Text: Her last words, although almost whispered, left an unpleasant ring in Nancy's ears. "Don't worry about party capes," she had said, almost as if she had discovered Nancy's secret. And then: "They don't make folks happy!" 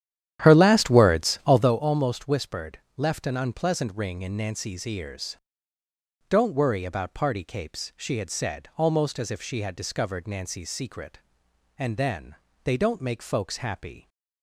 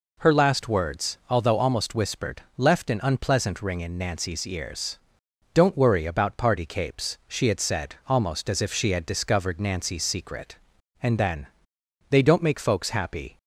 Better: second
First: starts louder than the rest; strong; until 1.8 s; 10.5 dB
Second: none

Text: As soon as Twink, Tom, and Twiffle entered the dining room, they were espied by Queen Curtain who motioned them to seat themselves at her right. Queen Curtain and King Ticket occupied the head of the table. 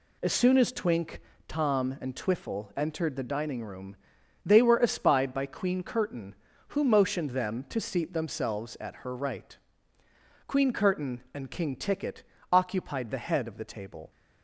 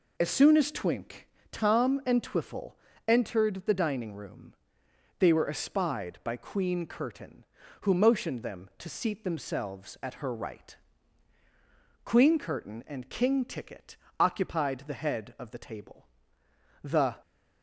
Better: first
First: pauses between "Ticket" and "occupied"; slight; at 12.2 s; 0.28 s long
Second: pauses between "Twiffle" and "entered"; slight; at 2.7 s; 0.34 s long // pauses between "Ticket" and "occupied"; slight; at 13.9 s; 0.22 s long // goes on to say "The"; slight; from 16.8 s on; 0.34 s long

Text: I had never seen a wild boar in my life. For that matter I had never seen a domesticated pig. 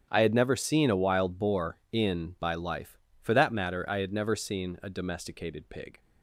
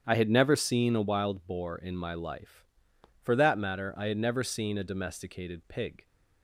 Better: second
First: starts louder than the rest; strong; until 1.1 s; 8.5 dB // says "by" for "my"; at 2.4 s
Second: starts louder than the rest; strong; until 1.0 s; 8.5 dB

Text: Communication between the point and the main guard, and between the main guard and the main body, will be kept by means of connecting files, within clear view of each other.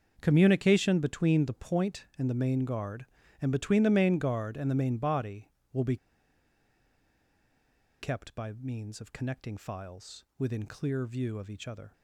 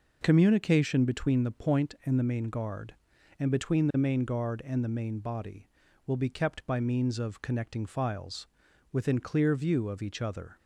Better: second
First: starts louder than the rest; until 1.2 s; 6.5 dB // pauses between "be" and "kept"; strong; at 5.9 s; 2.0 s long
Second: none

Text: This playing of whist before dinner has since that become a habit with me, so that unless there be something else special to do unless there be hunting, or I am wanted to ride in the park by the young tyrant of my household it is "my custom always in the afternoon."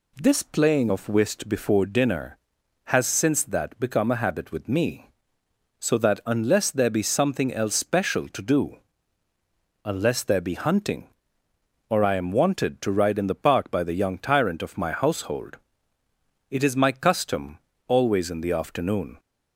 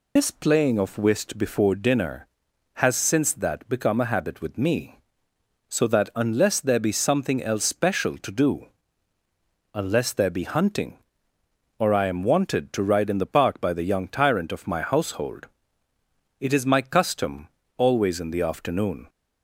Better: first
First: pauses between "do" and "unless"; at 8.7 s; 1.0 s long // pauses between "household" and "it"; noticeable; at 15.5 s; 0.92 s long // pauses between "custom" and "always"; slight; at 17.5 s; 0.28 s long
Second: loses the start of "This"; at 0.1 s; 120 ms // pauses between "do" and "unless"; at 8.6 s; 1.0 s long // pauses between "household" and "it"; noticeable; at 15.4 s; 0.92 s long // pauses between "custom" and "always"; slight; at 17.4 s; 0.28 s long

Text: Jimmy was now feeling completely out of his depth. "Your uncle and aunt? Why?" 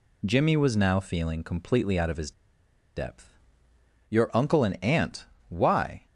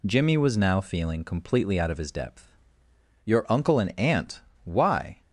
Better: second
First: pauses between "his" and "depth"; noticeable; at 2.3 s; 0.64 s long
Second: none

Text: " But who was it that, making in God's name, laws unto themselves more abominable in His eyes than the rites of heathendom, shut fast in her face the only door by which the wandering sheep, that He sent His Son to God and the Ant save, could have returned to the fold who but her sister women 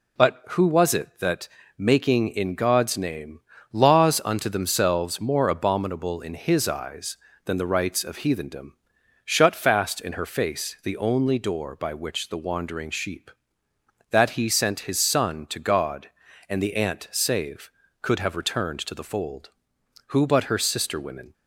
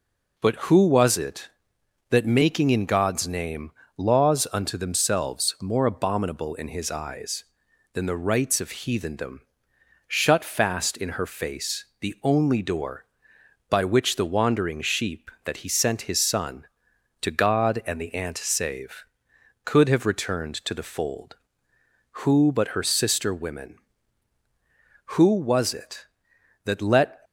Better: first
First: none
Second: pauses between "face" and "the"; slight; at 11.8 s; 0.16 s long // goes on to say "Who was it that let"; strong; from 25.1 s on; 2.0 s long

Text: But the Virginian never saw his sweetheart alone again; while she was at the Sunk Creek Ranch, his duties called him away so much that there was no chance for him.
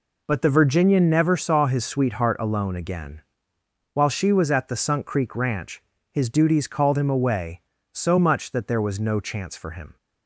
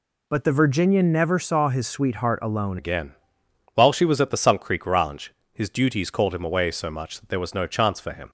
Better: first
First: none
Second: changes voice at "again"; from 2.7 s on; 5.5 s long

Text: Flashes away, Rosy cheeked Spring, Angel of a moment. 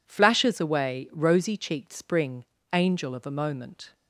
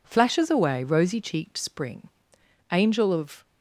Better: first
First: none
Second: stops before "a moment"; at 3.4 s

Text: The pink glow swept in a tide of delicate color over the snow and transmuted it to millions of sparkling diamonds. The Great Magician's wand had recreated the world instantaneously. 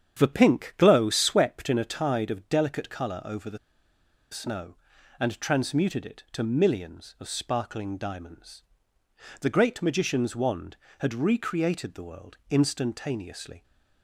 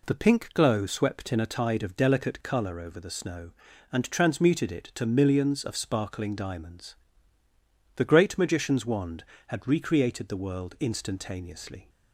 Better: second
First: starts louder than the rest; strong; until 1.2 s; 8.5 dB // pauses between "the" and "snow"; noticeable; at 3.5 s; 0.74 s long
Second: none

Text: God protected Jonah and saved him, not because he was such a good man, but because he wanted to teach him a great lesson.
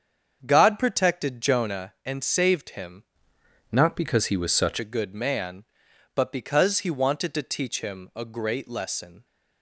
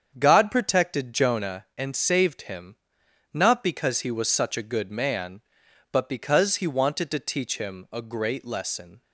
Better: second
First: starts louder than the rest; strong; until 1.4 s; 7 dB // changes voice from "not" to "such"; from 3.7 to 4.7 s; 1.0 s long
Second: starts louder than the rest; strong; until 1.2 s; 7.5 dB

